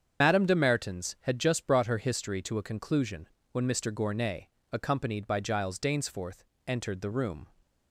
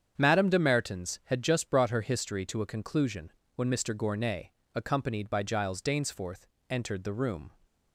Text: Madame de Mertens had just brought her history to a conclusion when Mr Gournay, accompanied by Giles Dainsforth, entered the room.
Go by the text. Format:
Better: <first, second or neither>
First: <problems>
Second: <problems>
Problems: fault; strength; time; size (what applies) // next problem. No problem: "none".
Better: second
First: loses the start of "Madame"; at 0.2 s; 65 ms // starts louder than the rest; strong; until 1.2 s; 7.5 dB // pauses between "conclusion" and "when"; slight; at 3.2 s; 0.22 s long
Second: starts louder than the rest; strong; until 1.1 s; 8 dB // pauses between "conclusion" and "when"; slight; at 3.3 s; 0.22 s long